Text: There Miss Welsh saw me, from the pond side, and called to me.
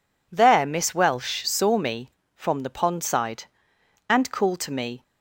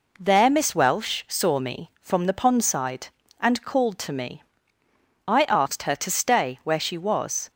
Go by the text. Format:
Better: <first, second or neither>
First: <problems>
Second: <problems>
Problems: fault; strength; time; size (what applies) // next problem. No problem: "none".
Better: first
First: none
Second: goes on to say "I asked her to stay where she was"; strong; from 5.2 s on; 2.2 s long